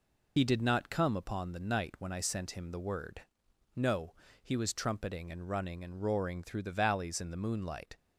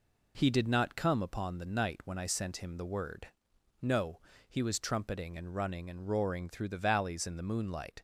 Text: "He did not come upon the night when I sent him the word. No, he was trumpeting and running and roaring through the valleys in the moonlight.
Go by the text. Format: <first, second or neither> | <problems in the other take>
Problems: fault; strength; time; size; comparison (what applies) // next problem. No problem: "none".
second | loses the start of "He"; at 0.3 s; 75 ms